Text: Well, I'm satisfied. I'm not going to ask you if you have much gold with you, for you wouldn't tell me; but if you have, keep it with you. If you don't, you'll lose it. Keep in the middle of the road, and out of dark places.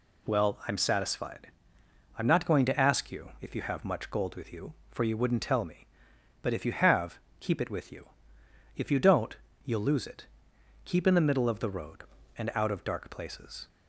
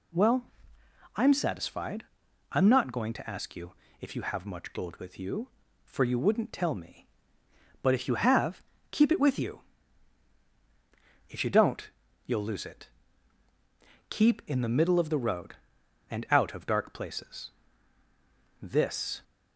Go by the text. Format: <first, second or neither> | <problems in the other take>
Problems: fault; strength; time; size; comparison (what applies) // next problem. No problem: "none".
first | pauses between "you" and "if"; slight; at 3.7 s; 0.26 s long // goes on to say "This"; noticeable; from 18.6 s on; 0.62 s long